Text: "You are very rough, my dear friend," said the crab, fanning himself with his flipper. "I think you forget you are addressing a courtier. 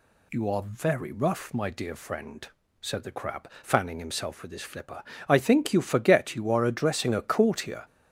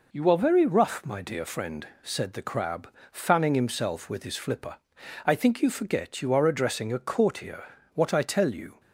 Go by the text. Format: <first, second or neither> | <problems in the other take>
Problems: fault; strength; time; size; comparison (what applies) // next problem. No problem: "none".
first | goes on to say "What I tell you"; noticeable; from 7.9 s on; 0.85 s long